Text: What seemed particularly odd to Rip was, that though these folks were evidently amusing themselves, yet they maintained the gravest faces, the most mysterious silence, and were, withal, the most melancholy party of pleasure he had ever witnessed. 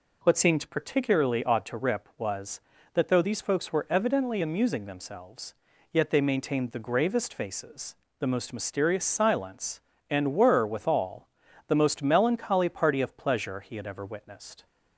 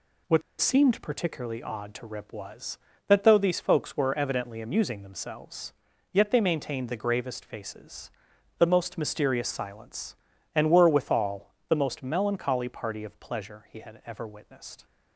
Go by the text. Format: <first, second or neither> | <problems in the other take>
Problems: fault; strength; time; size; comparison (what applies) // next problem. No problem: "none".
first | pauses between "What" and "seemed"; slight; at 0.4 s; 0.17 s long